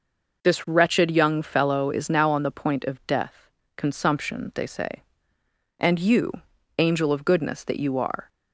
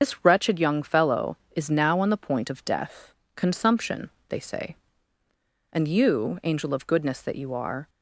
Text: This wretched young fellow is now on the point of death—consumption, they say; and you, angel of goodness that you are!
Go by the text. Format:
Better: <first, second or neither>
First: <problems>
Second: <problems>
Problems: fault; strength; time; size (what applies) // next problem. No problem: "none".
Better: first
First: none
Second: loses the start of "This"; at 0.0 s; 65 ms // starts louder than the rest; until 1.0 s; 6.5 dB